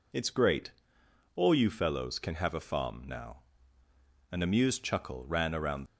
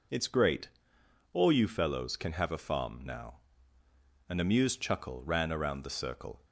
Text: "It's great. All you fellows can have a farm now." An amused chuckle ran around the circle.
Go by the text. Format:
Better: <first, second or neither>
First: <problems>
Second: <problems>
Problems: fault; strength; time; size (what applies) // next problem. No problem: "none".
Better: second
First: stops before "the circle"; at 5.8 s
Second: none